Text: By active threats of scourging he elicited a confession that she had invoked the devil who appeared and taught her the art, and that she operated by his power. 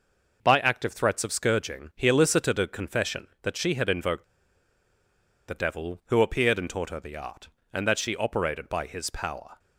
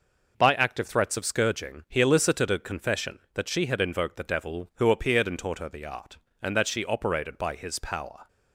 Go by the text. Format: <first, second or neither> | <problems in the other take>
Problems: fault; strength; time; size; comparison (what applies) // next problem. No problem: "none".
second | pauses between "invoked" and "the"; at 4.2 s; 1.2 s long